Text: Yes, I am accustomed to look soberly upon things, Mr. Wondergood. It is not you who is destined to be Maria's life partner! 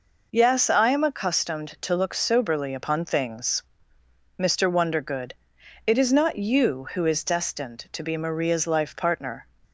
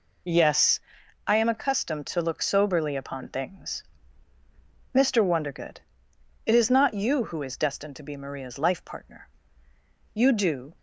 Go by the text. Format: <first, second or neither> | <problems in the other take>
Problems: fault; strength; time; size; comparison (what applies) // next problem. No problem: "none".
first | goes on to say "You do"; from 10.1 s on; 0.60 s long